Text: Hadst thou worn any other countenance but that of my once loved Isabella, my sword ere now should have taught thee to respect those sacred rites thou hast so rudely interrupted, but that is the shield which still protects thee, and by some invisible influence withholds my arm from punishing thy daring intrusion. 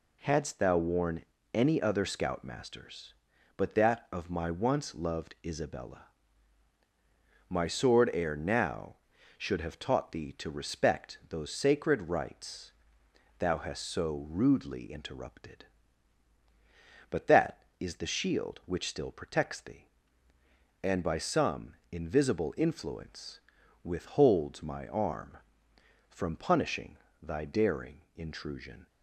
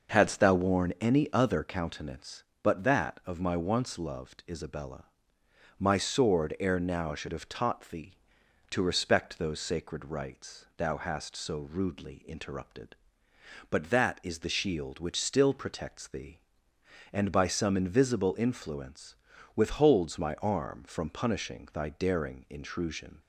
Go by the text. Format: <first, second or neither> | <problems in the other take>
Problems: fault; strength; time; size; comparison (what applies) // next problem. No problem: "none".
second | pauses between "worn" and "any"; slight; at 1.2 s; 0.30 s long // says "scoutmasters" for "countenance"; at 2.0 s // pauses between "rites" and "thou"; noticeable; at 12.7 s; 0.66 s long // pauses between "some" and "invisible"; slight; at 21.7 s; 0.16 s long // pauses between "influence" and "withholds"; at 23.3 s; 0.44 s long; also in the second // pauses between "punishing" and "thy"; slight; at 26.9 s; 0.24 s long // pauses between "daring" and "intrusion"; slight; at 28.0 s; 0.16 s long